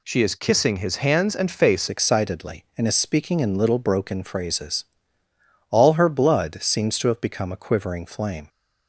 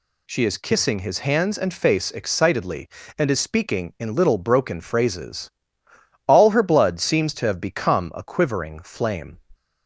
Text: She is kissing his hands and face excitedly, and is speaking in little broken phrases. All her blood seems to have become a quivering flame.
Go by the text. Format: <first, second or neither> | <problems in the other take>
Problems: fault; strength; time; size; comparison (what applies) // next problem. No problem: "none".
second | changes voice at "excitedly"; from 1.8 s on; 6.6 s long